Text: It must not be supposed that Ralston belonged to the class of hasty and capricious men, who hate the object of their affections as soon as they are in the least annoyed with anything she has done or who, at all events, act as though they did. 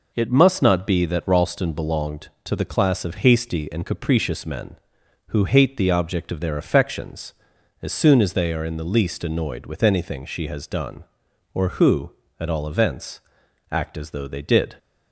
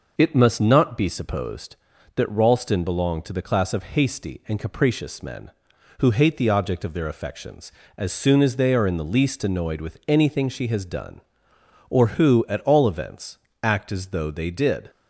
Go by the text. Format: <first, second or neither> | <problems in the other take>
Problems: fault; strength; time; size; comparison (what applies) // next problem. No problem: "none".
second | skips "supposed"; at 1.0 s